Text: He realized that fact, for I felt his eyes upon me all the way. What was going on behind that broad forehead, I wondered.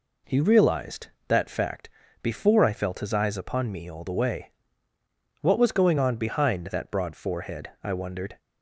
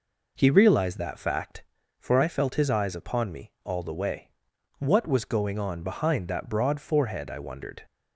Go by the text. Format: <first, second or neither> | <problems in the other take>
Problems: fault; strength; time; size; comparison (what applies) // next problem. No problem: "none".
second | says "before" for "for"; at 2.2 s